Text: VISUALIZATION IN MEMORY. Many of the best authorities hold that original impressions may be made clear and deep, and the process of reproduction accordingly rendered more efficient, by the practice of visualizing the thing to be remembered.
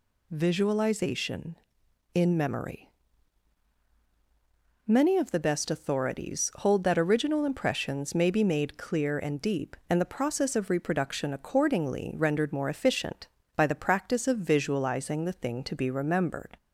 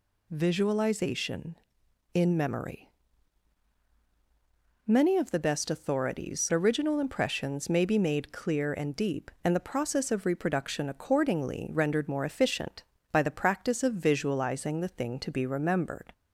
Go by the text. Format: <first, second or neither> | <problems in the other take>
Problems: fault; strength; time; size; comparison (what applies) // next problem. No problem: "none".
first | skips "hold that"; at 6.5 s